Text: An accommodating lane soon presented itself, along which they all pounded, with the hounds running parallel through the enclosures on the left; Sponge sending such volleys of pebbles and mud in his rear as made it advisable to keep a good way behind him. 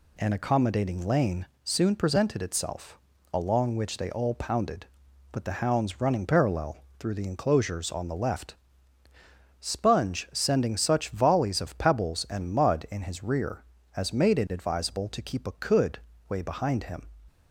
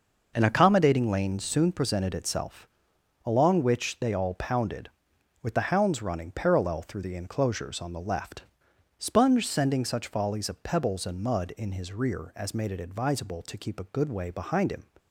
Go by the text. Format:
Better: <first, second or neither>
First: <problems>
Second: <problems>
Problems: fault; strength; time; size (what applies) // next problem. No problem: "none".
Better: second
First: pauses between "lane" and "soon"; slight; at 1.4 s; 0.18 s long // pauses between "parallel" and "through"; slight; at 6.7 s; 0.20 s long // says "could" for "good"; at 15.5 s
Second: none